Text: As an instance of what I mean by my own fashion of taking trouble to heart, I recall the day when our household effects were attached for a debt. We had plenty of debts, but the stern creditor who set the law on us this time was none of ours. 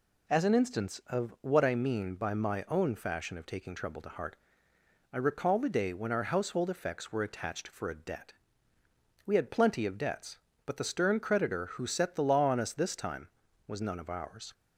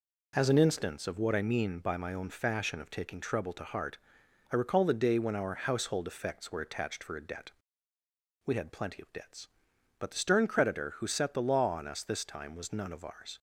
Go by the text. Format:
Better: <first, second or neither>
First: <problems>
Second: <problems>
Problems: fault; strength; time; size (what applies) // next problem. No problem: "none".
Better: neither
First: none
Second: none